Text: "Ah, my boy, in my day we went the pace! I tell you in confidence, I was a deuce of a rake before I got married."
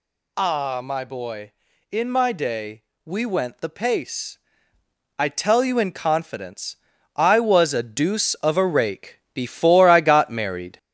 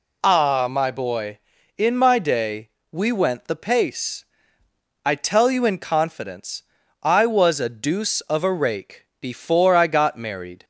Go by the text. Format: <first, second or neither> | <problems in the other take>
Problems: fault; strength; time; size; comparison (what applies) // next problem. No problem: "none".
second | gets louder; slight; throughout; 3.5 dB // pauses between "day" and "we"; slight; at 2.8 s; 0.20 s long; slight in the second // pauses between "rake" and "before"; slight; at 9.1 s; 0.16 s long; slight in the second